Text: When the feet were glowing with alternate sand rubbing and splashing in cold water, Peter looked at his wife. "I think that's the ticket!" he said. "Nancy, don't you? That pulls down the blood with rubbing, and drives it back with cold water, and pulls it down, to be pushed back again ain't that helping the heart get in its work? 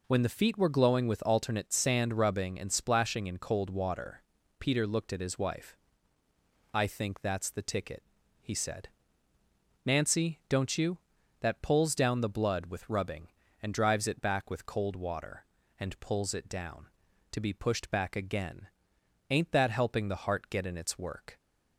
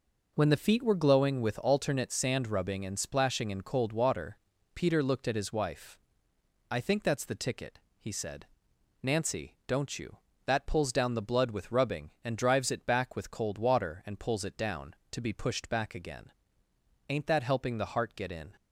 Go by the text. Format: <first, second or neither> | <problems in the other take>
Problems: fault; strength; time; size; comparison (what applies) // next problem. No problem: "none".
first | pauses between "again" and "ain't"; noticeable; at 16.3 s; 0.78 s long; noticeable in the first // stops before "its work"; at 18.5 s